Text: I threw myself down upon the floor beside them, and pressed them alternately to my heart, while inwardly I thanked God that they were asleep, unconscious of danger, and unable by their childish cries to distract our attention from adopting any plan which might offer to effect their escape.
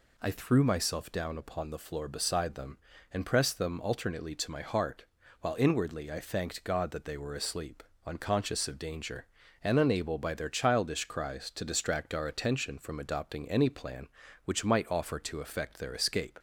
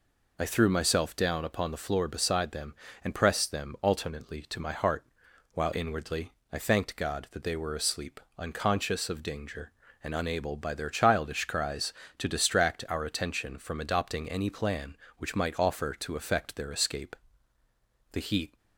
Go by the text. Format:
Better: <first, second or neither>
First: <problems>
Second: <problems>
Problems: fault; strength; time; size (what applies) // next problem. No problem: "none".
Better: first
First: none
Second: pauses between "inwardly" and "I"; slight; at 6.3 s; 0.22 s long // goes on to say "The heat"; slight; from 18.1 s on; 0.46 s long